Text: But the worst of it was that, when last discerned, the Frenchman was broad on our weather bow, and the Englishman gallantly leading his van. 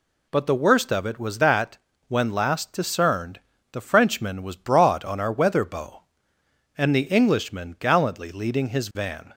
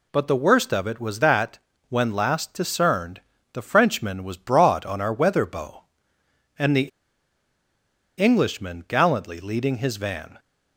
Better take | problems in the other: first | pauses between "the" and "Englishman"; strong; at 6.8 s; 1.2 s long

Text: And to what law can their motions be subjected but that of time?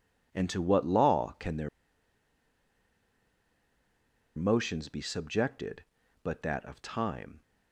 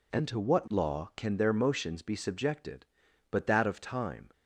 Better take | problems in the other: second | pauses between "their" and "motions"; strong; at 1.6 s; 2.6 s long

